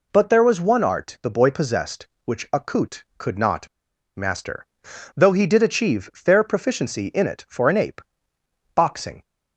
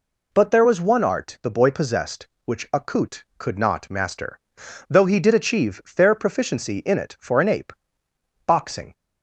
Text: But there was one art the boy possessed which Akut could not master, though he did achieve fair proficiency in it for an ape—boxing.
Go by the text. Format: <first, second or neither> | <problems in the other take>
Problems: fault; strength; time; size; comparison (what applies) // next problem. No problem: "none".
second | pauses between "not" and "master"; noticeable; at 3.6 s; 0.48 s long